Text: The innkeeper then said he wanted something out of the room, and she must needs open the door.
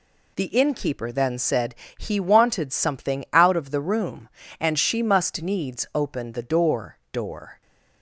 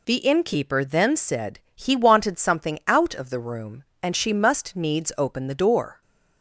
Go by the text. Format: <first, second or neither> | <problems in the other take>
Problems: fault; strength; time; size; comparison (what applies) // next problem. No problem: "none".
second | pauses between "said" and "he"; slight; at 1.7 s; 0.24 s long; slight in the second // says "door" twice; at 7.1 s